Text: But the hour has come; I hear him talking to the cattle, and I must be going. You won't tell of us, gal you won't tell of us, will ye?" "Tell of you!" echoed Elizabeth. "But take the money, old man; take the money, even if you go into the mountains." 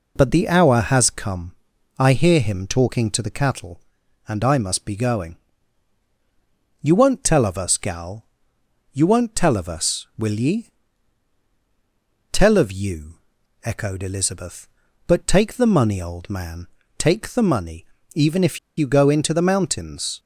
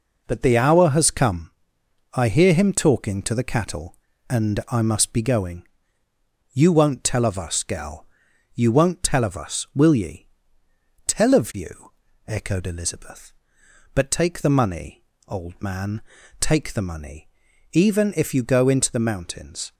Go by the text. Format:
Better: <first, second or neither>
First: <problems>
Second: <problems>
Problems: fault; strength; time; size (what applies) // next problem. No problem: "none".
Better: second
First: pauses between "gal" and "you"; noticeable; at 8.2 s; 0.70 s long // pauses between "if" and "you"; slight; at 18.5 s; 0.18 s long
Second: pauses between "gal" and "you"; noticeable; at 8.0 s; 0.50 s long